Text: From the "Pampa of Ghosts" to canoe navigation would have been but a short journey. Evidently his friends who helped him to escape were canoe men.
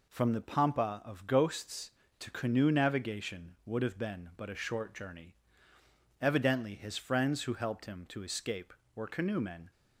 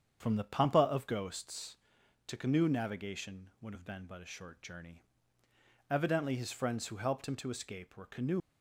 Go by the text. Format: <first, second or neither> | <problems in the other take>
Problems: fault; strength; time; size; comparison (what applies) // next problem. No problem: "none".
first | starts louder than the rest; strong; until 1.2 s; 8 dB // stops before "men"; at 8.4 s